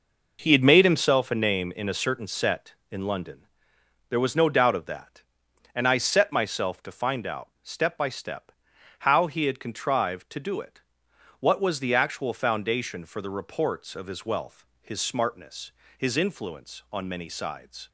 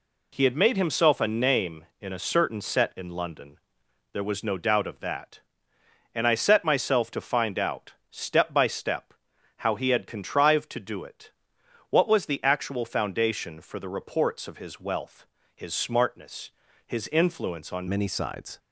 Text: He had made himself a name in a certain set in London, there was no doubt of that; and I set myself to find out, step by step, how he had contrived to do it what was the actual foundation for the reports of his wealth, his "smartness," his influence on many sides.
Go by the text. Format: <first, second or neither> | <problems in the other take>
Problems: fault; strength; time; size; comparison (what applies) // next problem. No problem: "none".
first | pauses between "it" and "what"; noticeable; at 11.2 s; 0.62 s long; noticeable in the first // changes voice at "many"; from 17.8 s on; 0.7 s long